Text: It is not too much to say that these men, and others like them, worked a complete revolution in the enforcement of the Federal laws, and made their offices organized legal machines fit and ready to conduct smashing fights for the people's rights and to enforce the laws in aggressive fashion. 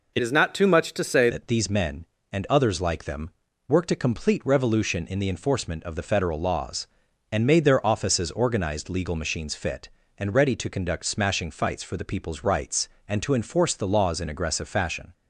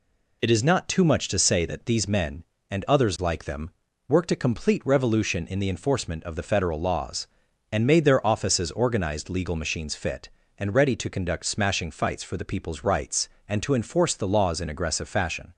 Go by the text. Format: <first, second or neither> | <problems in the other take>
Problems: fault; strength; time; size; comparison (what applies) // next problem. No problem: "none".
second | changes voice from "is" to "say"; from 0.2 to 1.2 s; 1.0 s long